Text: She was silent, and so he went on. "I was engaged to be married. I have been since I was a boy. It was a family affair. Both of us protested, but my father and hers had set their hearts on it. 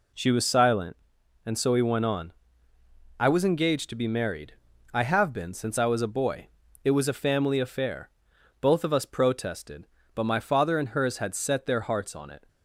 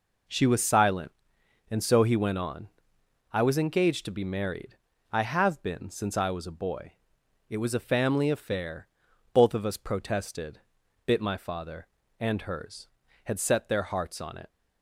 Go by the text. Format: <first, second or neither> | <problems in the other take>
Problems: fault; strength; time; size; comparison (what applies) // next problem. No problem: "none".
first | says "bit" for "but"; at 11.0 s